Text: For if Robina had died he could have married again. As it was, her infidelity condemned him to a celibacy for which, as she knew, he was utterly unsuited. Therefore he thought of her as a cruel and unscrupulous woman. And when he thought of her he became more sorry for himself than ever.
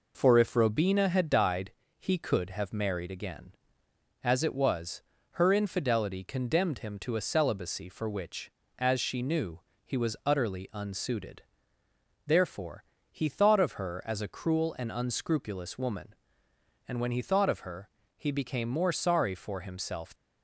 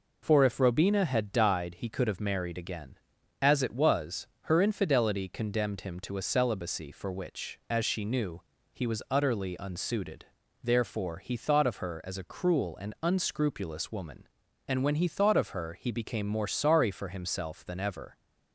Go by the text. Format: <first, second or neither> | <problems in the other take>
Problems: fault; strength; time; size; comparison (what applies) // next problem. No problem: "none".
second | pauses between "died" and "he"; slight; at 1.7 s; 0.26 s long // pauses between "Therefore" and "he"; slight; at 12.8 s; 0.30 s long // pauses between "her" and "he"; slight; at 17.8 s; 0.26 s long // stops before "than ever"; at 20.1 s